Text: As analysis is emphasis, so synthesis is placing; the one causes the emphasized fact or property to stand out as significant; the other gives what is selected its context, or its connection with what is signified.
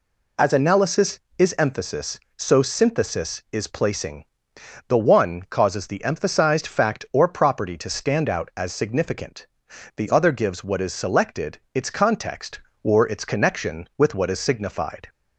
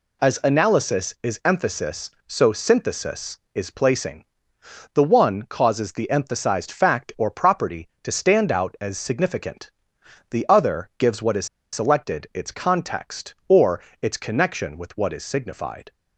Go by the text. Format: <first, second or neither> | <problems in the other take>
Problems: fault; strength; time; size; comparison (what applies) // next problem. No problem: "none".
first | pauses between "is" and "selected"; slight; at 11.4 s; 0.27 s long // pauses between "or" and "its"; slight; at 13.7 s; 0.22 s long